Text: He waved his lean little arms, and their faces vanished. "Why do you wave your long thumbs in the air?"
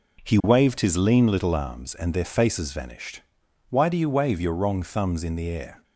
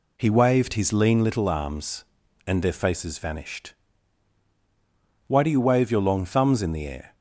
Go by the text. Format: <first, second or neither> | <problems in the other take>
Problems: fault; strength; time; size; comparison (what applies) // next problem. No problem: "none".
second | says "wrong" for "long"; at 4.5 s